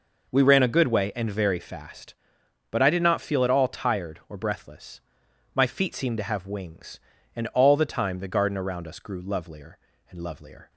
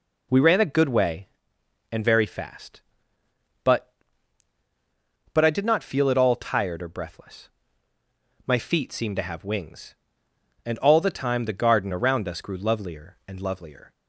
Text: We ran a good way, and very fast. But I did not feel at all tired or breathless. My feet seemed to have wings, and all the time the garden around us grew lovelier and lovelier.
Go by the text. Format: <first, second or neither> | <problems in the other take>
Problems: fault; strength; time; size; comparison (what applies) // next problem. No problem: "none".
first | says "But" twice; at 5.3 s